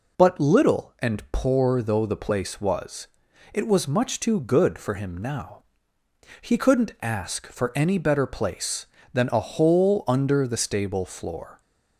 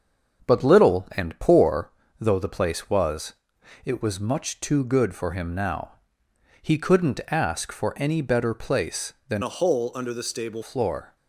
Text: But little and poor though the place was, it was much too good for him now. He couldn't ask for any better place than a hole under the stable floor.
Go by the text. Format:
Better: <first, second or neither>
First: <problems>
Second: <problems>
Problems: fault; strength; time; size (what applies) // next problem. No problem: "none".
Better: first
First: none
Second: starts louder than the rest; until 1.5 s; 6.5 dB // pauses between "poor" and "though"; slight; at 1.9 s; 0.28 s long // changes voice from "a" to "stable"; from 9.4 to 10.6 s; 1.2 s long